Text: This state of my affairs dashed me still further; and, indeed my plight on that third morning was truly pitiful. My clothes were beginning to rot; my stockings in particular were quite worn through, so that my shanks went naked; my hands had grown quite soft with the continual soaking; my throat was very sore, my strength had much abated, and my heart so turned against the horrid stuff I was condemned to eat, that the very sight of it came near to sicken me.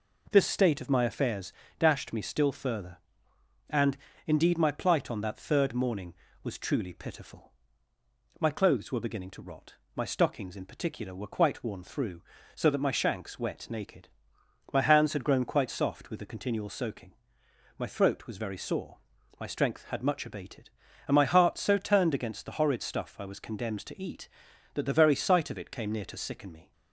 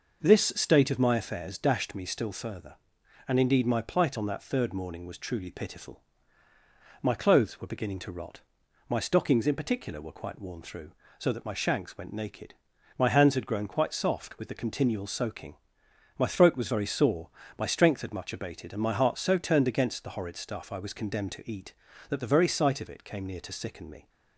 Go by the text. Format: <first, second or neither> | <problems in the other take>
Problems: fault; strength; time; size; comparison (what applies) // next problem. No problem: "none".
second | pauses between "affairs" and "dashed"; slight; at 1.5 s; 0.25 s long // says "wet" for "went"; at 13.3 s